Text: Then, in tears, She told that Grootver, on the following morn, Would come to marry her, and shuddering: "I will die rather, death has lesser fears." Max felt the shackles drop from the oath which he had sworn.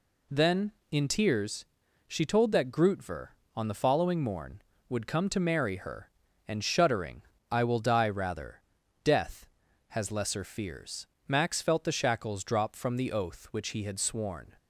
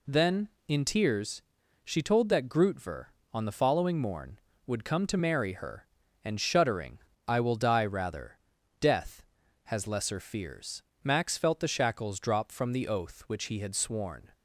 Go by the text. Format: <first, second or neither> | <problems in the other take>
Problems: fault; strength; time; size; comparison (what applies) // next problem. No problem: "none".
neither | none